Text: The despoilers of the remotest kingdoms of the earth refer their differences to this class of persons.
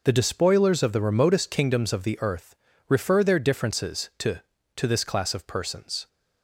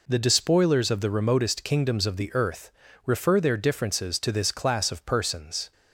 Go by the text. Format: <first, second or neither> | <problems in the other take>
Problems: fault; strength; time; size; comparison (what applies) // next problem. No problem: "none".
second | pauses between "earth" and "refer"; slight; at 2.5 s; 0.32 s long; slight in the second // says "to" twice; at 4.7 s